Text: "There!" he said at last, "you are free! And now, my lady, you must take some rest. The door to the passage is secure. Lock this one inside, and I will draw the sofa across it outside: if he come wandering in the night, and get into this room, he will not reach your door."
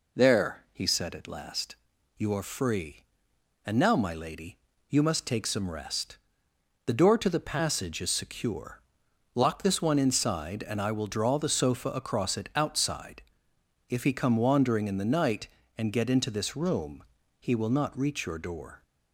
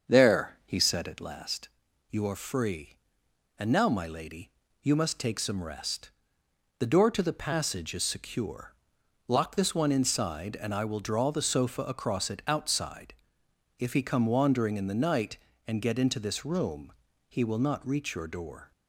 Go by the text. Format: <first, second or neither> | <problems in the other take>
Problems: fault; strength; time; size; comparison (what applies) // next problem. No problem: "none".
first | starts louder than the rest; until 1.4 s; 7 dB